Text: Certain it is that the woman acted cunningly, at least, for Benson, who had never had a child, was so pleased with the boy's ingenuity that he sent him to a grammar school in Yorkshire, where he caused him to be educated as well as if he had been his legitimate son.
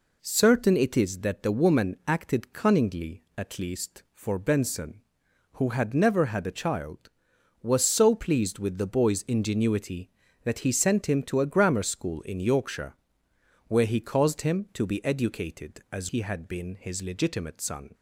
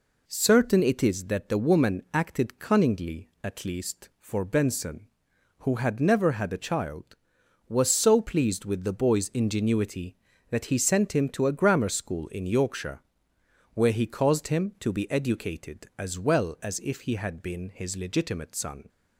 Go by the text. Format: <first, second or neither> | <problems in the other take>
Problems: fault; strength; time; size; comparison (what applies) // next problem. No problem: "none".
second | skips "well as if"; at 16.0 s